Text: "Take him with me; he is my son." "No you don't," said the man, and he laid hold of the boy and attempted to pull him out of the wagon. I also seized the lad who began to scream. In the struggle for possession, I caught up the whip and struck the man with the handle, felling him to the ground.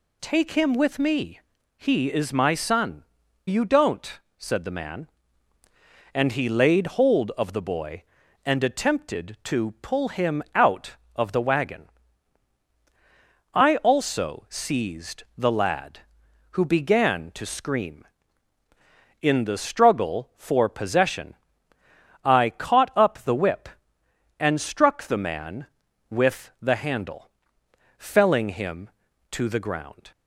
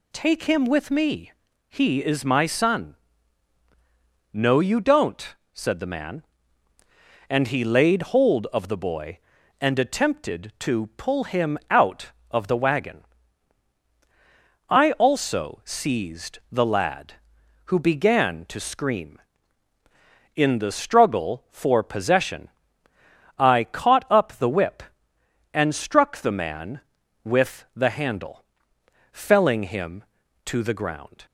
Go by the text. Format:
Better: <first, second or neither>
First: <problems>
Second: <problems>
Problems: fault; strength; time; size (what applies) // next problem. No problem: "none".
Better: second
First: skips "No"; at 3.2 s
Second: none